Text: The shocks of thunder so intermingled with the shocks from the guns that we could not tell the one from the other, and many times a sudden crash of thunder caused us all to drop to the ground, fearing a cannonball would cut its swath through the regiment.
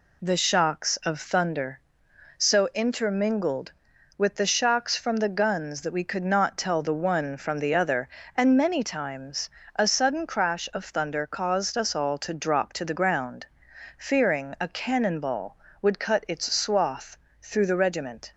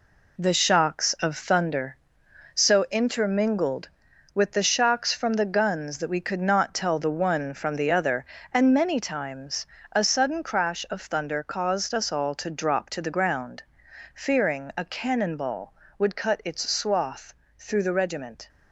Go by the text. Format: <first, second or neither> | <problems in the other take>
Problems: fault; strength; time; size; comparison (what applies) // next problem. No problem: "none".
first | gets quieter; strong; throughout; 8 dB // pauses between "times" and "a"; slight; at 9.6 s; 0.26 s long; slight in the first // pauses between "swath" and "through"; slight; at 17.3 s; 0.24 s long; slight in the first